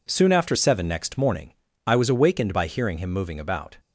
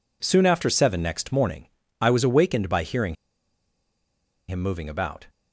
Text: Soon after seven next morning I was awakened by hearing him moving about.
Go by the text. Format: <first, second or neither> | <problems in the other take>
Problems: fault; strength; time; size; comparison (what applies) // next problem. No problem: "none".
first | pauses between "morning" and "I"; slight; at 1.6 s; 0.32 s long; slight in the first // pauses between "hearing" and "him"; strong; at 3.1 s; 1.3 s long